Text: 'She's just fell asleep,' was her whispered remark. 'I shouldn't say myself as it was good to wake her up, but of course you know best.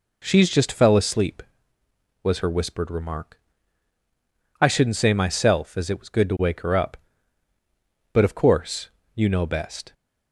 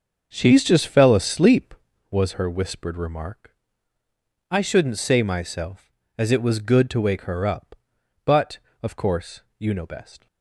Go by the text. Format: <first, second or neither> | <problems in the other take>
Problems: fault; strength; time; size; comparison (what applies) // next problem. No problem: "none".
first | starts louder than the rest; until 2.2 s; 6.5 dB // pauses between "course" and "you"; slight; at 9.4 s; 0.16 s long; slight in the first